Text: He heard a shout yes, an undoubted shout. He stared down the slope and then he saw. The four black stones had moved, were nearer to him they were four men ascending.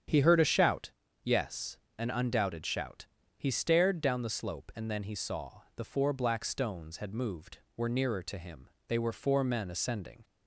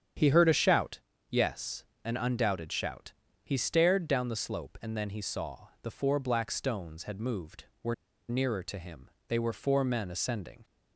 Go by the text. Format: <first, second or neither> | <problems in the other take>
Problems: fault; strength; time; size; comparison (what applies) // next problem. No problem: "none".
first | starts louder than the rest; strong; until 1.5 s; 8.5 dB; strong in the first // pauses between "shout" and "yes"; slight; at 0.9 s; 0.32 s long; slight in the first // pauses between "were" and "nearer"; slight; at 7.9 s; 0.35 s long // pauses between "him" and "they"; slight; at 9.0 s; 0.22 s long; slight in the first